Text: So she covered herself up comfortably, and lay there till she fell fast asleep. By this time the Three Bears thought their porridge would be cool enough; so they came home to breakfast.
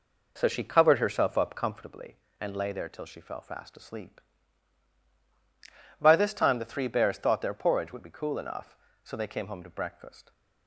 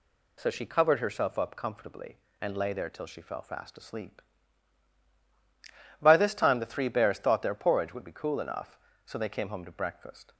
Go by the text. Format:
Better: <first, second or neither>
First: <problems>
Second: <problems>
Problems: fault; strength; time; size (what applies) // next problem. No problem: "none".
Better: second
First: starts louder than the rest; noticeable; until 1.9 s; 4 dB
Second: none